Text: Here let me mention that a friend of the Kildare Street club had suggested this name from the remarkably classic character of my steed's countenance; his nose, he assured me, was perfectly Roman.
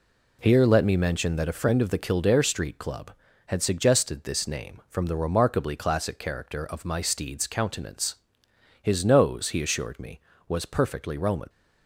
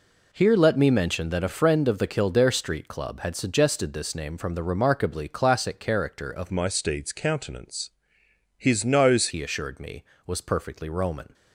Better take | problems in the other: first | changes voice from "my" to "nose"; from 6.5 to 9.2 s; 2.7 s long

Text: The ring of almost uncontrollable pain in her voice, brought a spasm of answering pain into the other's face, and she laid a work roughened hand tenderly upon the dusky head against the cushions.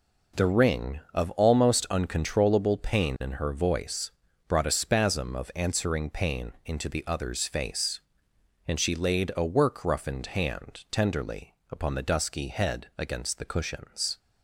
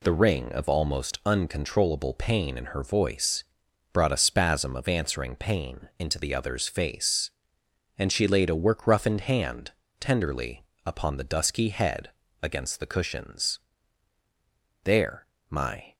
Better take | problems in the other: first | pauses between "hand" and "tenderly"; slight; at 9.7 s; 0.30 s long // pauses between "tenderly" and "upon"; slight; at 10.6 s; 0.20 s long; slight in the first // pauses between "head" and "against"; slight; at 12.1 s; 0.30 s long // goes on to say "There my"; noticeable; from 14.8 s on; 1.1 s long

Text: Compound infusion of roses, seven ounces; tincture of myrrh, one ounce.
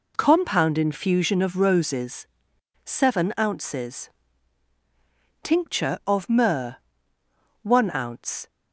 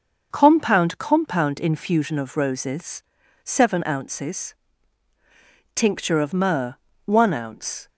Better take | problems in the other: first | starts louder than the rest; until 1.3 s; 6 dB // says "Compound" twice; at 0.9 s

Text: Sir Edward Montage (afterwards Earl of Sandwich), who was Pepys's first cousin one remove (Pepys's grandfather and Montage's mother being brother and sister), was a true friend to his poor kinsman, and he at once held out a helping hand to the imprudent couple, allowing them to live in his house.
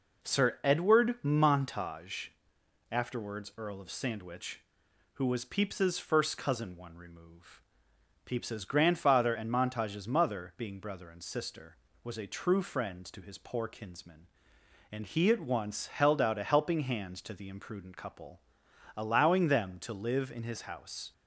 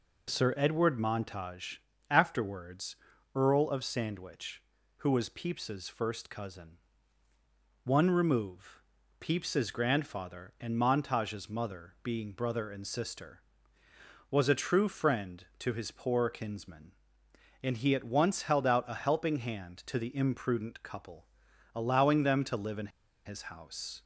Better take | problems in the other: first | pauses between "afterwards" and "Earl"; at 2.9 s; 0.38 s long // pauses between "cousin" and "one"; at 6.7 s; 1.0 s long // pauses between "in" and "his"; at 22.9 s; 0.36 s long

